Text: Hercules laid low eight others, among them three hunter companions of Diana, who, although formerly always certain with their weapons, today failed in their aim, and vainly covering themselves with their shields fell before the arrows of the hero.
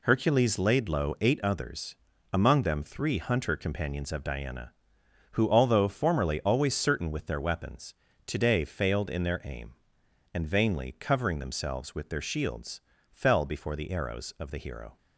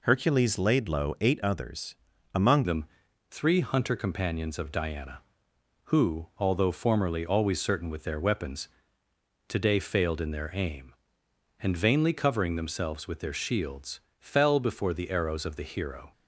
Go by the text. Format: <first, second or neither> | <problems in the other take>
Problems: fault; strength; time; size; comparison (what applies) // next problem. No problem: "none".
first | changes voice at "them"; from 2.6 s on; 13.5 s long // pauses between "them" and "three"; at 2.8 s; 0.44 s long // pauses between "shields" and "fell"; slight; at 13.9 s; 0.20 s long; slight in the first